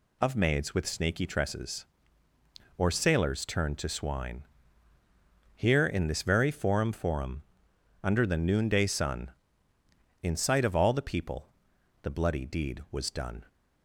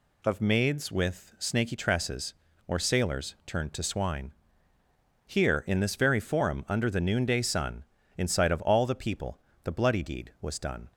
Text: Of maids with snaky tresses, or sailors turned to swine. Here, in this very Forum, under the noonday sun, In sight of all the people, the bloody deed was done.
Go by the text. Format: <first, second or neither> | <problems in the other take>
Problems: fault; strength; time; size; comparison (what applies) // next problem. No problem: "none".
second | says "Forum" twice; at 6.9 s